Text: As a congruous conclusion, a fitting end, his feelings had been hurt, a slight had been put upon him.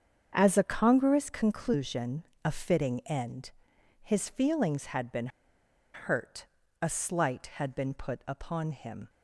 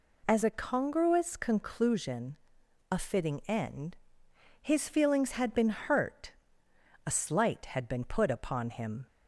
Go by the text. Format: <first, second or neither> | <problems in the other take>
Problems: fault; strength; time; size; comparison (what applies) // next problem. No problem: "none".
second | starts louder than the rest; strong; until 1.3 s; 7.5 dB // pauses between "been" and "hurt"; noticeable; at 5.2 s; 0.66 s long